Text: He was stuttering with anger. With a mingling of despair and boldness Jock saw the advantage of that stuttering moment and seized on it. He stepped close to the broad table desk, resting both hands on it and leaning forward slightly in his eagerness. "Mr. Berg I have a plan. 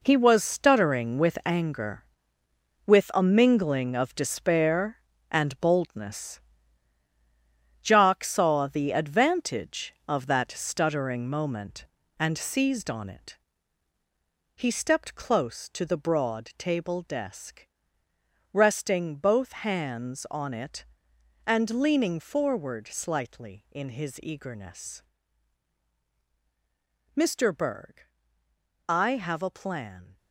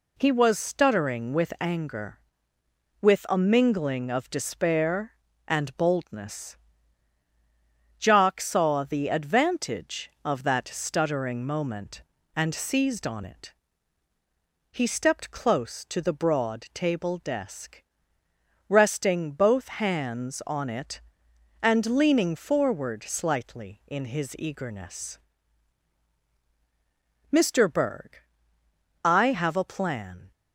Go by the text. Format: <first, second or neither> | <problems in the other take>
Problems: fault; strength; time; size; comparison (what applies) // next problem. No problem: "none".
second | gets quieter; strong; throughout; 10.5 dB // pauses between "boldness" and "Jock"; strong; at 6.4 s; 1.4 s long; strong in the second // pauses between "Berg" and "I"; noticeable; at 28.0 s; 0.86 s long; noticeable in the second